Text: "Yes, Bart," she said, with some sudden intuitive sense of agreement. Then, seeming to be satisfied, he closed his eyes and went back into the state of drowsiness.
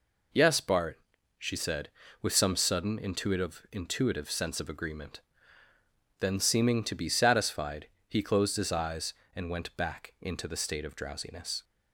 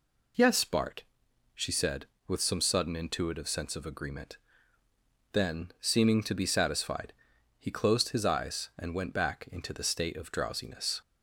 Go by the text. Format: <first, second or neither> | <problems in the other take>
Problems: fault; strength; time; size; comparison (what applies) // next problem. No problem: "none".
second | says "intuitive" twice; at 3.7 s